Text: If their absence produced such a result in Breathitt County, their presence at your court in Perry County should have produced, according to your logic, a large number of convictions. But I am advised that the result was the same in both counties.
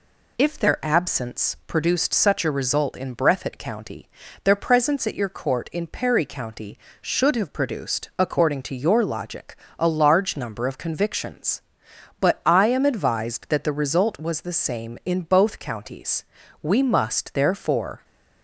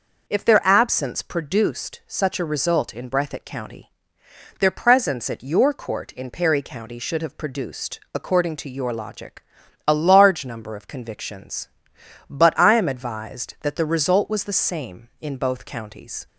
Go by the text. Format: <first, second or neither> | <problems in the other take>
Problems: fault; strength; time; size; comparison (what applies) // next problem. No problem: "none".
second | goes on to say "We must therefore"; from 16.6 s on; 1.4 s long